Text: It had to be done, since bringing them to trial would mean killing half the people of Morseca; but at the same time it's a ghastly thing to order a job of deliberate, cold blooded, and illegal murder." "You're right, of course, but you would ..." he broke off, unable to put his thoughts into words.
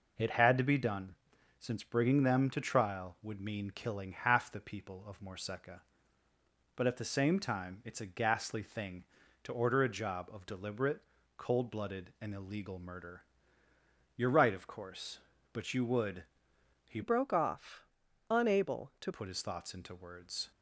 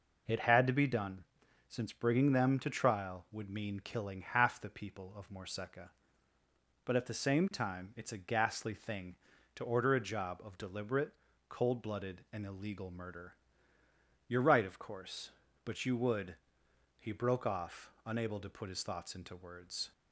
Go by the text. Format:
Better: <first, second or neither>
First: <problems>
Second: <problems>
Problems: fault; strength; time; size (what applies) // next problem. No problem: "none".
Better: second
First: changes voice from "broke" to "to"; from 17.0 to 19.1 s; 2.1 s long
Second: none